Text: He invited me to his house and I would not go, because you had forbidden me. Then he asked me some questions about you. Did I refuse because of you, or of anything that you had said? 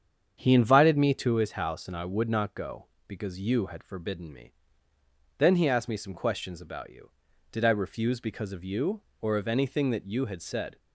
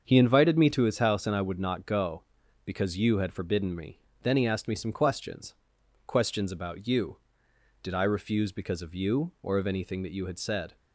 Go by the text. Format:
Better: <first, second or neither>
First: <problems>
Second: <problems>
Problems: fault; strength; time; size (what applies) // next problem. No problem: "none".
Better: first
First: starts louder than the rest; strong; until 1.4 s; 8 dB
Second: starts louder than the rest; until 1.0 s; 7 dB // says "questions" twice; at 6.0 s